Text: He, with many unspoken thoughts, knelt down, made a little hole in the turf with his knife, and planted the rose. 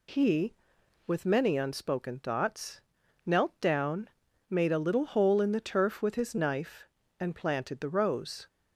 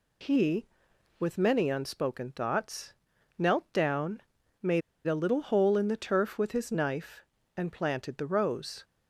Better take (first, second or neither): first